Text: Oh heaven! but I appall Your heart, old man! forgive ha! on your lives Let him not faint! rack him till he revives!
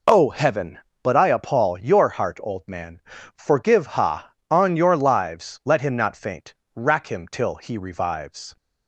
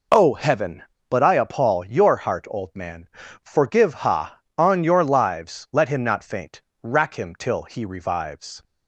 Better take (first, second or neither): neither